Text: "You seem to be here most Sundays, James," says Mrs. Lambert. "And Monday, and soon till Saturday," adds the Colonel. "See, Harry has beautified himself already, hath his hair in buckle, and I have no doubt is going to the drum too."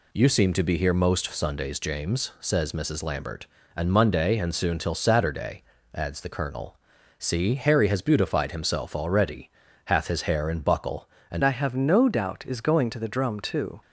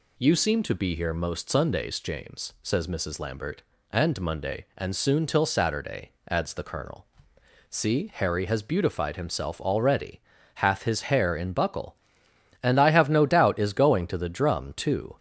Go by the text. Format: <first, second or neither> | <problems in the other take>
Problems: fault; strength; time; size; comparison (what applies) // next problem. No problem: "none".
second | changes voice at "I"; from 11.4 s on; 2.4 s long